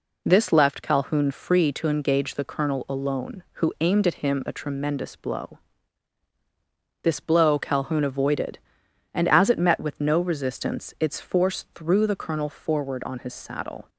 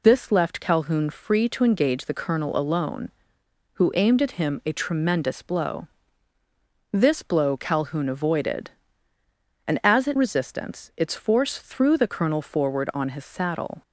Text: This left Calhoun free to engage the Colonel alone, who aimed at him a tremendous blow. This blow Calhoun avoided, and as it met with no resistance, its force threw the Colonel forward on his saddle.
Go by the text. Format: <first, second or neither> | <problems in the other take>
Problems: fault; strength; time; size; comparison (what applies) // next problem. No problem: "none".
first | skips "met with no"; at 10.1 s